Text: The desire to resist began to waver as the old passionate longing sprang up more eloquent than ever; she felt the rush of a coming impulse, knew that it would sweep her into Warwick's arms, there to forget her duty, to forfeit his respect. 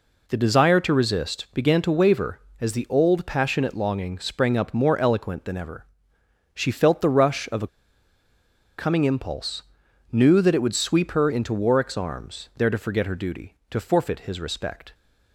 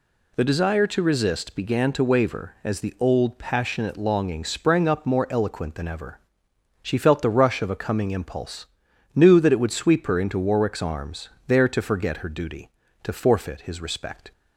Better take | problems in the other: second | pauses between "a" and "coming"; at 7.6 s; 1.1 s long

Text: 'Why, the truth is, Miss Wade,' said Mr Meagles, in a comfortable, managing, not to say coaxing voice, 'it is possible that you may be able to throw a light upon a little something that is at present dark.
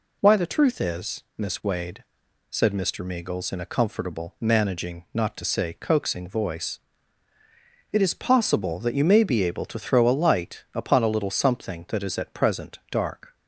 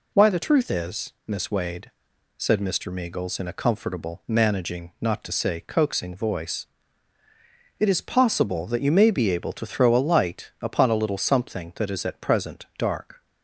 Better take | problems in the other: neither | none

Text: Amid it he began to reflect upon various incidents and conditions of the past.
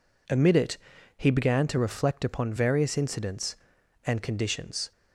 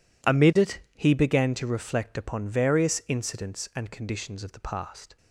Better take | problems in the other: second | pauses between "it" and "he"; at 0.7 s; 0.40 s long; slight in the second // stops before "of the past"; at 4.9 s

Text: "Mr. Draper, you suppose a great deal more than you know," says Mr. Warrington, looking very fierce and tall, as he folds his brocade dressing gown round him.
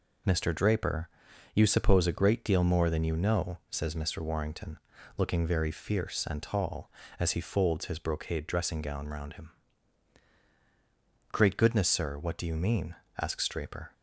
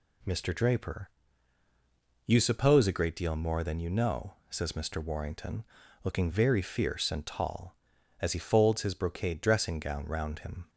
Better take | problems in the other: second | goes on to say "Great goodness sir what do you mean asks Draper"; strong; from 11.3 s on; 2.6 s long

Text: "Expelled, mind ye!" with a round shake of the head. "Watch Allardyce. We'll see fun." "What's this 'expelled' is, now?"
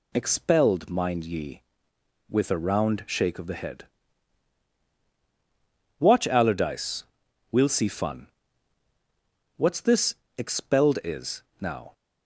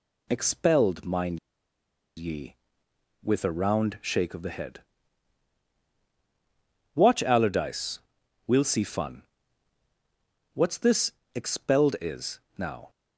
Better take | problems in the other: first | pauses between "mind" and "ye"; noticeable; at 1.3 s; 0.79 s long // pauses between "this" and "expelled"; slight; at 11.1 s; 0.24 s long; slight in the first

